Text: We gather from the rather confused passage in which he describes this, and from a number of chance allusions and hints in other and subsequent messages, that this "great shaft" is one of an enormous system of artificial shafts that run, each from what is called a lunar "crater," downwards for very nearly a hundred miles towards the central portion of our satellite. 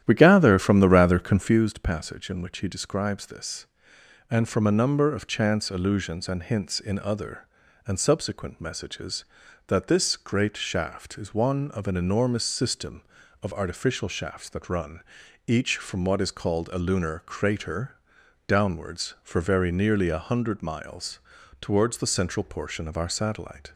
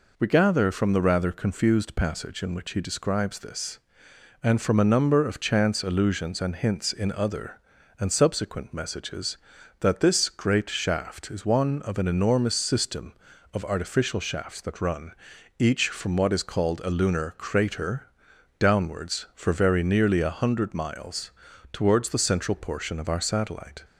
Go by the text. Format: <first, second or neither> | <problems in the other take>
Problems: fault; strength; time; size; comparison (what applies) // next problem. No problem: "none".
second | starts louder than the rest; strong; until 1.7 s; 11 dB // pauses between "miles" and "towards"; at 21.1 s; 0.40 s long; also in the second